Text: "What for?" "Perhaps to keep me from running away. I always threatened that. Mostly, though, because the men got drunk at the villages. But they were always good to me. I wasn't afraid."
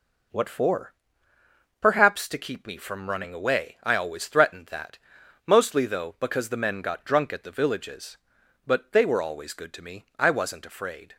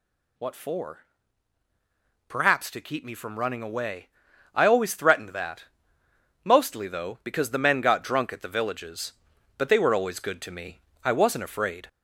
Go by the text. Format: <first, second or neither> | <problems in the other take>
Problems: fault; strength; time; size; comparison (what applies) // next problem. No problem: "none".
first | gets louder; slight; throughout; 2.5 dB